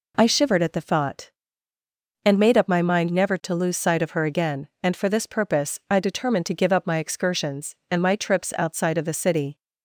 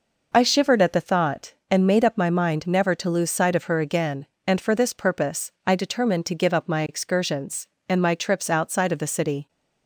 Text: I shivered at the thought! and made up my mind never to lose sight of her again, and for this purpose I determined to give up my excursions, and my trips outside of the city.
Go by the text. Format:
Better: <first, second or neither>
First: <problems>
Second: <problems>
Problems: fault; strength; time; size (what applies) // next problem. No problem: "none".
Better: neither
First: none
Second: none